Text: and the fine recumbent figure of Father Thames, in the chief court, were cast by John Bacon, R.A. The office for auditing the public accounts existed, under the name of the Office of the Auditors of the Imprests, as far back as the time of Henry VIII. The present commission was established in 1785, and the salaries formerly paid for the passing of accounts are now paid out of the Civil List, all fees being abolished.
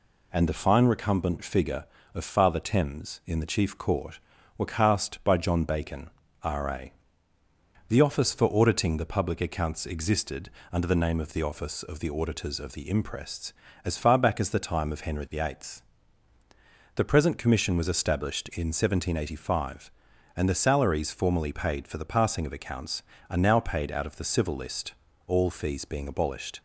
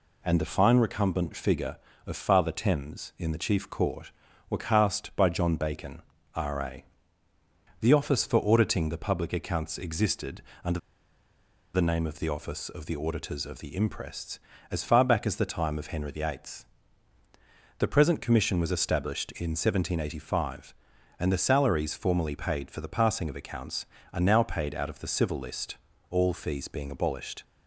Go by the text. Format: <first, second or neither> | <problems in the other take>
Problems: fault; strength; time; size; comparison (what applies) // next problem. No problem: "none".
first | pauses between "under" and "the"; noticeable; at 10.7 s; 0.95 s long